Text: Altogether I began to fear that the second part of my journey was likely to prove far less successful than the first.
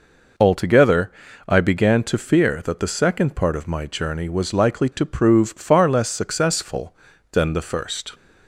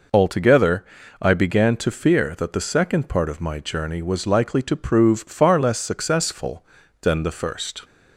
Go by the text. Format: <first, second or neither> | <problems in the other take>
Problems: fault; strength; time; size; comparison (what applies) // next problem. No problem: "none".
neither | pauses between "Altogether" and "I"; the same in both